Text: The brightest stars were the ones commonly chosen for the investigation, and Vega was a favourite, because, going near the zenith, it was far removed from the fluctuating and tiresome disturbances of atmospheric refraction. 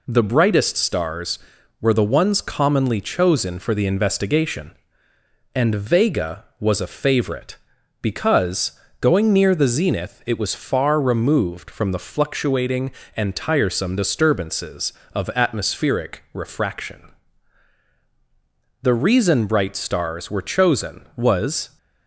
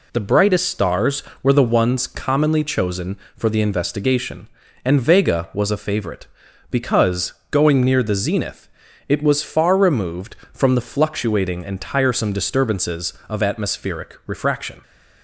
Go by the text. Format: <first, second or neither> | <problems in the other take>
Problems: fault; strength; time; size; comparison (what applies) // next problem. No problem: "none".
second | goes on to say "The reason bright stars were chosen was"; strong; from 18.8 s on; 2.9 s long